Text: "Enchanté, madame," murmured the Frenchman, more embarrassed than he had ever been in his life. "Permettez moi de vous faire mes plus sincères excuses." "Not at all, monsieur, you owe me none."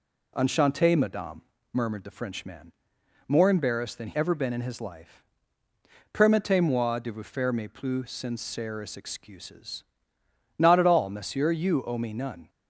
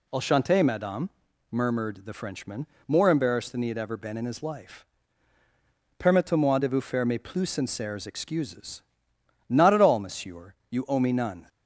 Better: second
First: skips "had"; at 4.1 s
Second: none

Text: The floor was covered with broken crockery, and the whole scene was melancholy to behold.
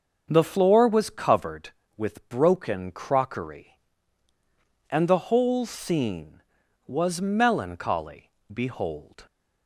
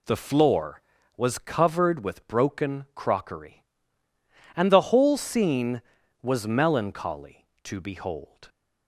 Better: second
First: starts louder than the rest; until 1.3 s; 6.5 dB // skips "to"; at 8.3 s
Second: none

